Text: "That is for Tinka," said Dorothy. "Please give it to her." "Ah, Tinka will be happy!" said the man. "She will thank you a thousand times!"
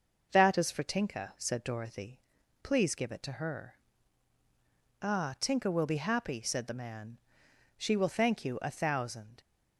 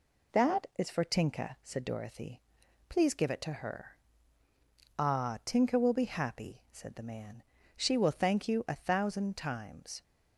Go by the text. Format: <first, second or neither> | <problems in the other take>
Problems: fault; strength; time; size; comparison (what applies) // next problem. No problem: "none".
second | stops before "times"; at 9.3 s